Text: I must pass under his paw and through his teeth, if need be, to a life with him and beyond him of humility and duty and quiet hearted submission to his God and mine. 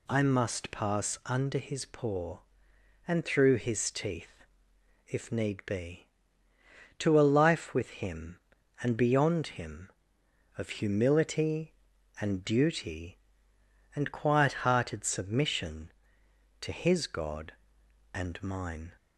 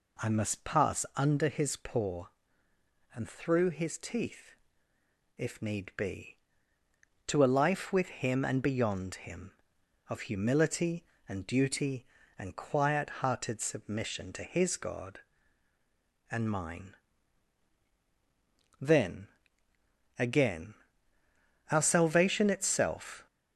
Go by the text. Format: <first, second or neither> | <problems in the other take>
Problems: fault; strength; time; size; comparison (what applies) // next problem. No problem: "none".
first | goes on to say "Then again our salvation itself"; strong; from 18.8 s on; 4.4 s long